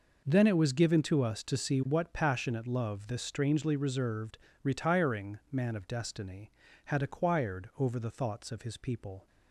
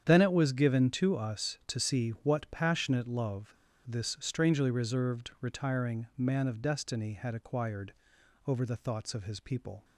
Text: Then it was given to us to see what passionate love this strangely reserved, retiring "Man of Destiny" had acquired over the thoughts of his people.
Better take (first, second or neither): first